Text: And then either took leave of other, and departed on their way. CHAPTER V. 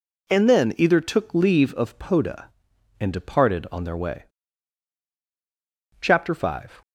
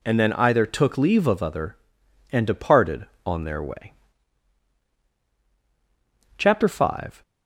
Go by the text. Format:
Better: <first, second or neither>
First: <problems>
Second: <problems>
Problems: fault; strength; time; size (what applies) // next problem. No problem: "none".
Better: second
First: says "poda" for "other"; at 1.9 s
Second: none